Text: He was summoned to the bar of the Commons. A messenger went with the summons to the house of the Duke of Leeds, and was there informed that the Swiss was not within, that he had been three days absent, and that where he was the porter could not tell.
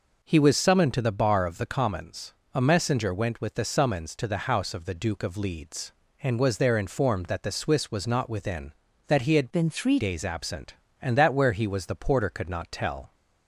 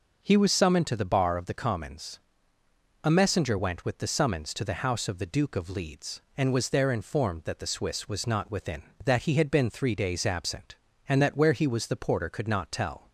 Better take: second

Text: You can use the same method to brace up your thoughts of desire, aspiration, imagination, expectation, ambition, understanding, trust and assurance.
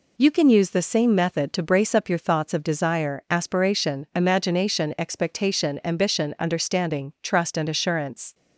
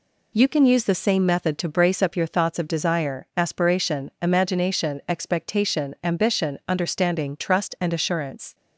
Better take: neither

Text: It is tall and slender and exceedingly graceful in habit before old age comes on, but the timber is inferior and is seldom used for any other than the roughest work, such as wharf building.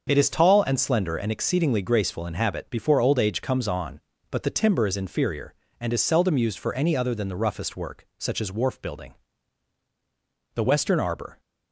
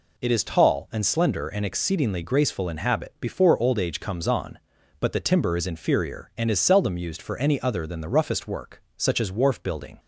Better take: second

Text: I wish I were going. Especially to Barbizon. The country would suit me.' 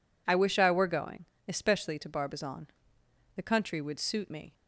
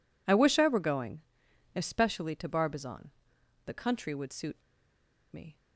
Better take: first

